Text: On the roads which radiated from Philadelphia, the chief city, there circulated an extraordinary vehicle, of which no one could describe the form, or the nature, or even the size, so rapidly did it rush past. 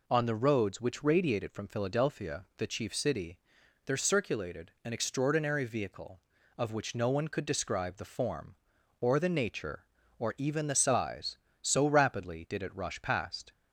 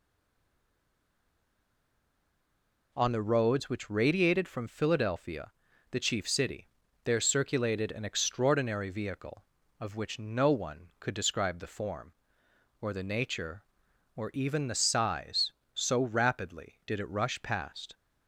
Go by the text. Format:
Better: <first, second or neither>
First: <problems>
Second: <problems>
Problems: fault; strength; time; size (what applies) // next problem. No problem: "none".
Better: first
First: none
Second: stays silent before the first word; strong; until 2.9 s; 2.9 s long